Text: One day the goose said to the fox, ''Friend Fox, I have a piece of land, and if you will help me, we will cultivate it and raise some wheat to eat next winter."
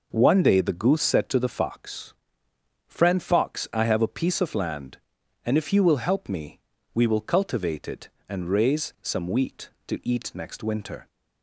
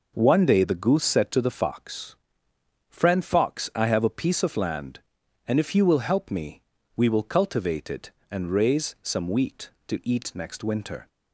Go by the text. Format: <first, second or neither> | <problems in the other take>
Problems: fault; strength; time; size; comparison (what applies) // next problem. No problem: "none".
neither | none